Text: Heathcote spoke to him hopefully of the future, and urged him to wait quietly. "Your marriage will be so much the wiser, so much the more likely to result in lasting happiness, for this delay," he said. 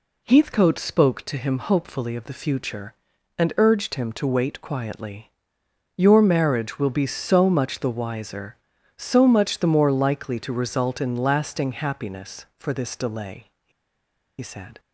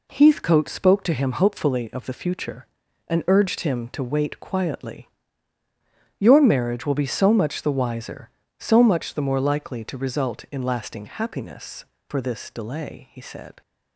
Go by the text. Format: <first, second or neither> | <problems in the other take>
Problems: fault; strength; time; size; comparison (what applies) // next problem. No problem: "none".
second | pauses between "he" and "said"; noticeable; at 13.7 s; 0.69 s long